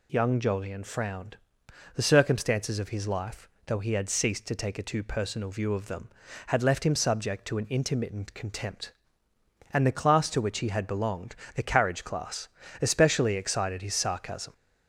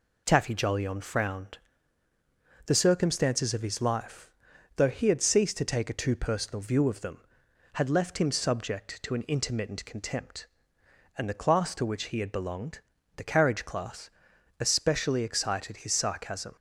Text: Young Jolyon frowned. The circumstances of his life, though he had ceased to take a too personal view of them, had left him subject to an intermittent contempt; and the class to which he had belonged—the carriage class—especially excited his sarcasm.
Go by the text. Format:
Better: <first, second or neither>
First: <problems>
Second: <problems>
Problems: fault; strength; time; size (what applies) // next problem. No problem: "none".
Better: first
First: none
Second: says "Taffy" for "Young"; at 0.2 s